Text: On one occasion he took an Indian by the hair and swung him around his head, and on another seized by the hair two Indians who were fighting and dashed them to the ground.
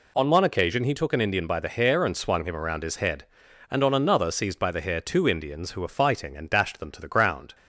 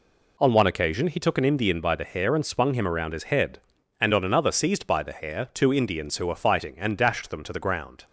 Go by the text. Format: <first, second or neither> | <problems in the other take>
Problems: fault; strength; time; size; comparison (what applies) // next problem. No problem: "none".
neither | none